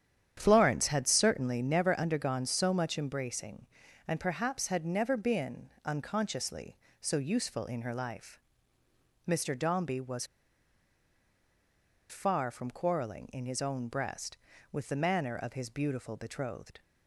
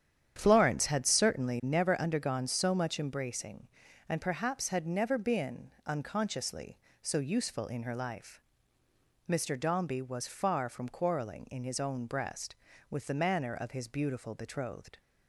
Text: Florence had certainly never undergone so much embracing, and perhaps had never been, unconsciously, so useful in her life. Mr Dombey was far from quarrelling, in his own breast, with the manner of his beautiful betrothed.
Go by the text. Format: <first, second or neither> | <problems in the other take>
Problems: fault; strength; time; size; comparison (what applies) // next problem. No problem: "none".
second | starts louder than the rest; strong; until 1.3 s; 9.5 dB; strong in the second // pauses between "was" and "far"; strong; at 10.2 s; 1.8 s long